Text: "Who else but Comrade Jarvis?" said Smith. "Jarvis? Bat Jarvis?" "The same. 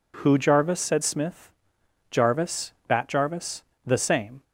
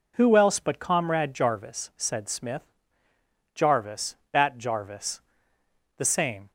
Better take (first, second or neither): second